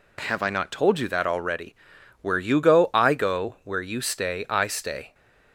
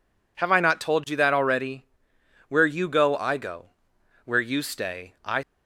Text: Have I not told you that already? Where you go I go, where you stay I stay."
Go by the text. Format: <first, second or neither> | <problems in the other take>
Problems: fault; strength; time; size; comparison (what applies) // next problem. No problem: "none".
first | stops before "stay"; at 5.4 s